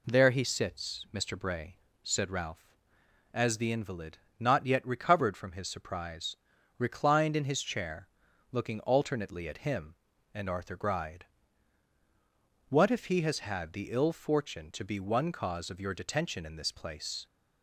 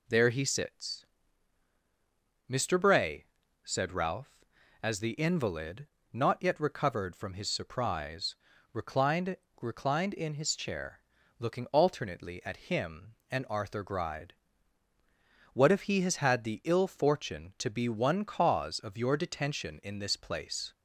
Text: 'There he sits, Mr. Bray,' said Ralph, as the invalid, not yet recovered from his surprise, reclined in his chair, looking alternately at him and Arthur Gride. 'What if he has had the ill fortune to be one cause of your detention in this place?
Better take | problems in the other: first | says "reclined" twice; at 9.6 s

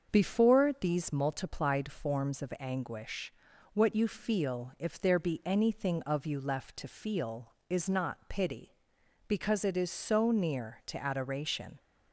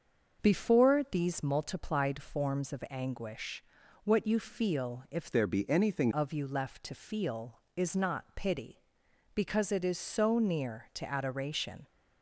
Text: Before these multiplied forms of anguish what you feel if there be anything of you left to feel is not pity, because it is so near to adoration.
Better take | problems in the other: first | starts louder than the rest; until 1.5 s; 6.5 dB; also in the first // pauses between "anguish" and "what"; at 3.6 s; 0.42 s long; also in the first // changes voice from "there" to "anything"; from 5.3 to 6.0 s; 0.7 s long

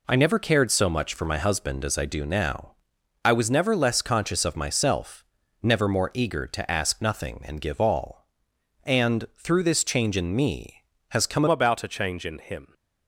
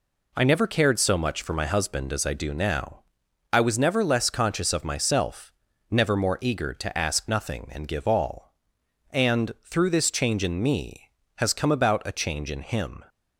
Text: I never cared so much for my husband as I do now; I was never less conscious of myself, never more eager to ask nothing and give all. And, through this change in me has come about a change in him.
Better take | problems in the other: second | changes voice at "about"; from 11.4 s on; 1.3 s long

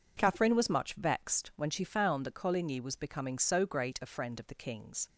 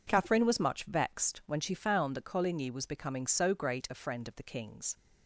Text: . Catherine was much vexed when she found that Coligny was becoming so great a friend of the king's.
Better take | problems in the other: neither | none

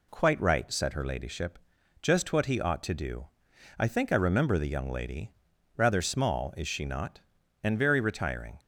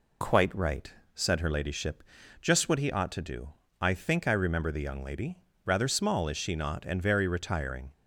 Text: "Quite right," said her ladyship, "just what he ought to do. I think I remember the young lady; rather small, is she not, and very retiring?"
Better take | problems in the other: neither | none

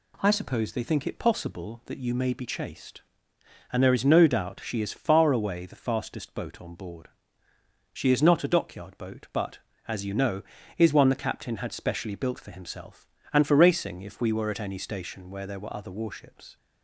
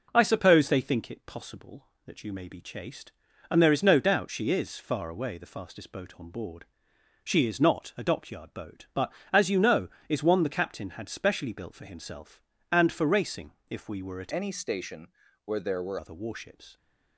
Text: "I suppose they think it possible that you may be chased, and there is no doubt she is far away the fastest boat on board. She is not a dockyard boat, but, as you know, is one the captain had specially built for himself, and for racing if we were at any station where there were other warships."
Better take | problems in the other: first | pauses between "racing" and "if"; slight; at 13.5 s; 0.18 s long // changes voice from "any" to "were"; from 14.3 to 15.9 s; 1.6 s long // pauses between "station" and "where"; slight; at 15.1 s; 0.32 s long

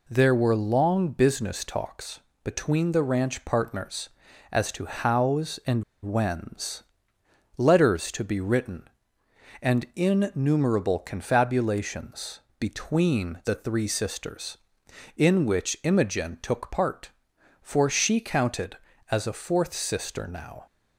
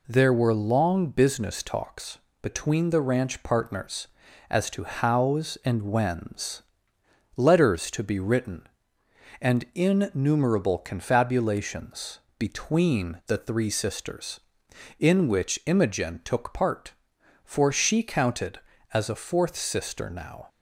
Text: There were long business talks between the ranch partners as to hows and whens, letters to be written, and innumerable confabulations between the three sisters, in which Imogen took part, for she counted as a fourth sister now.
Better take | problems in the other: second | pauses between "talks" and "between"; slight; at 2.2 s; 0.24 s long; slight in the second // pauses between "and" and "whens"; slight; at 5.8 s; 0.20 s long // pauses between "confabulations" and "between"; slight; at 12.3 s; 0.18 s long; slight in the second

